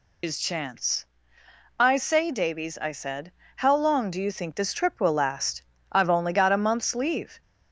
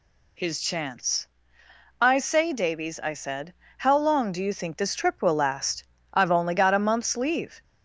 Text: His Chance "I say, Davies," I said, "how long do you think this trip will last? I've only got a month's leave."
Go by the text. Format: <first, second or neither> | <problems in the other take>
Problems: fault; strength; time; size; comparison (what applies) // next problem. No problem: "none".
second | loses the start of "His"; at 0.2 s; 70 ms // pauses between "Chance" and "I"; noticeable; at 1.0 s; 0.74 s long; noticeable in the second